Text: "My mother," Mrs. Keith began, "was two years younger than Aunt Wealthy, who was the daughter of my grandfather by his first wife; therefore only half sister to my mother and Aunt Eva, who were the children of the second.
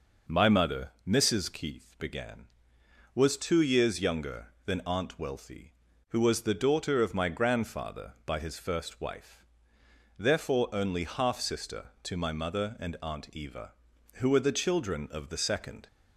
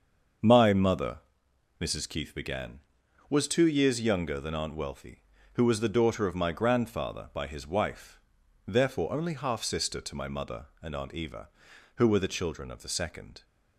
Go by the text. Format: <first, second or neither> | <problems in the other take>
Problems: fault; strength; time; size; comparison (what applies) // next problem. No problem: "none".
first | starts louder than the rest; until 2.0 s; 6.5 dB // skips "first"; at 7.6 s